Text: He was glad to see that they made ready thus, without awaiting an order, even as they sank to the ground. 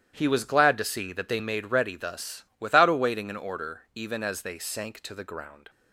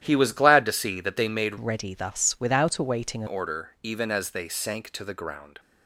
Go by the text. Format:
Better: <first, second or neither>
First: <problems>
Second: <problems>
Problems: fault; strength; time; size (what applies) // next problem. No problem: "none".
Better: first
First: starts louder than the rest; strong; until 1.1 s; 11.5 dB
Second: starts louder than the rest; strong; until 1.0 s; 11.5 dB // changes voice from "ready" to "an"; from 1.5 to 3.2 s; 1.7 s long